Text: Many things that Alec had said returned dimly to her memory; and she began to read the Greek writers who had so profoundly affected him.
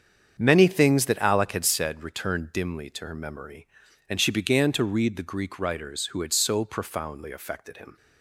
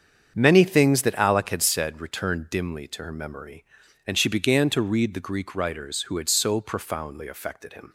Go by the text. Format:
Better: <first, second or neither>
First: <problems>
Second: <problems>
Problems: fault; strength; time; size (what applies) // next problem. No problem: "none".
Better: neither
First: starts louder than the rest; strong; until 1.3 s; 7.5 dB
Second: starts louder than the rest; strong; until 1.3 s; 7.5 dB